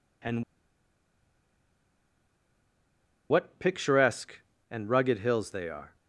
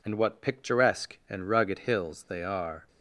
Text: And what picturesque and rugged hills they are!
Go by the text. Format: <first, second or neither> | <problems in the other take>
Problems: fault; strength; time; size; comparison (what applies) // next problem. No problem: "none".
second | pauses between "And" and "what"; strong; at 0.4 s; 2.8 s long